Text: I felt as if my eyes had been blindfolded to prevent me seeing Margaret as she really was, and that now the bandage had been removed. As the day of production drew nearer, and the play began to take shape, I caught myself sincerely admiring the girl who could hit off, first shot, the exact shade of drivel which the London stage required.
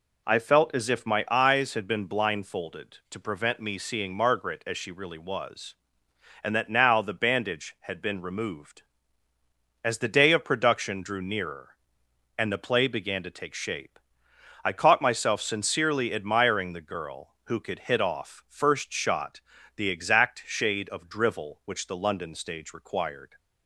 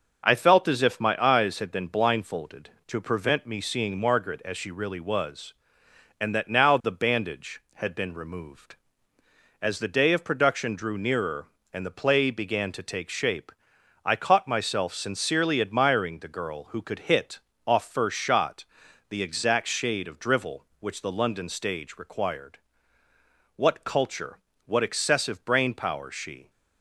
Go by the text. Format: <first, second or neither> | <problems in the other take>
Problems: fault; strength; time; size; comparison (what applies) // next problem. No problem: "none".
first | starts louder than the rest; until 1.2 s; 6 dB // pauses between "hit" and "off"; slight; at 17.3 s; 0.26 s long // goes on to say "What culture what excessive brain power she"; strong; from 23.5 s on; 2.9 s long